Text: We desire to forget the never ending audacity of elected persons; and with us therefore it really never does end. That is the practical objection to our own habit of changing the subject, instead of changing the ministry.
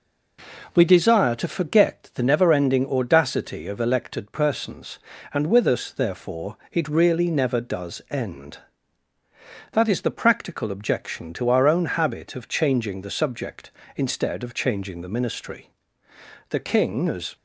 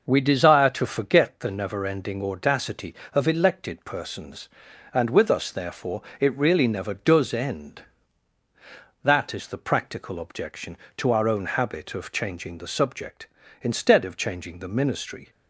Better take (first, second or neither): second